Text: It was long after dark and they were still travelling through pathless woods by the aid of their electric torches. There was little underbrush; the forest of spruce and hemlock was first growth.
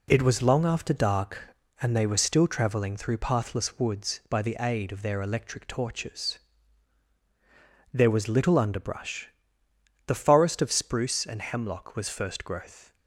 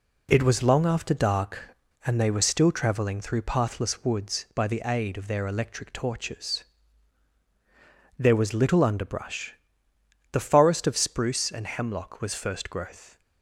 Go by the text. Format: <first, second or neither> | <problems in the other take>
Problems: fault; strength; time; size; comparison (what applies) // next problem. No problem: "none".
neither | none